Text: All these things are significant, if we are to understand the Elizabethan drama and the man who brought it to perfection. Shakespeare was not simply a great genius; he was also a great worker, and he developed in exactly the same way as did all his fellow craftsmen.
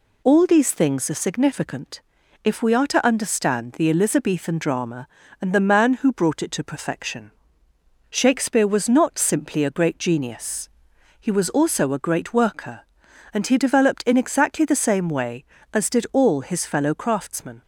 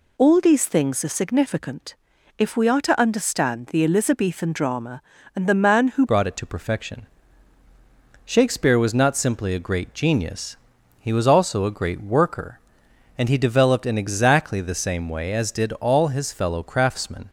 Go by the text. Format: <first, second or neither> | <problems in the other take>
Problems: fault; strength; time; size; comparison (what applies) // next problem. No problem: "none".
first | changes voice at "brought"; from 6.0 s on; 11.2 s long